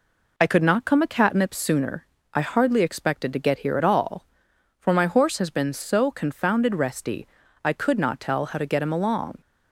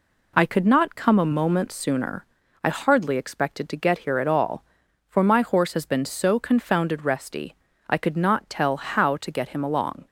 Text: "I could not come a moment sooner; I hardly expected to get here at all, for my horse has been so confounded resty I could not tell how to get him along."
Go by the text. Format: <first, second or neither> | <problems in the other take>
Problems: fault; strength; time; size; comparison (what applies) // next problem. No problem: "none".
second | says "catnip" for "moment"; at 1.0 s // pauses between "resty" and "I"; slight; at 7.2 s; 0.36 s long; slight in the second